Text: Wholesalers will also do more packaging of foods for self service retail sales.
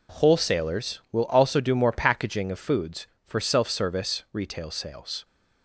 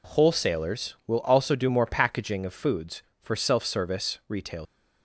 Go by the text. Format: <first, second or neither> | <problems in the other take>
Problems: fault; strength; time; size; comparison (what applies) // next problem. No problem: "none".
first | stops before "sales"; at 4.6 s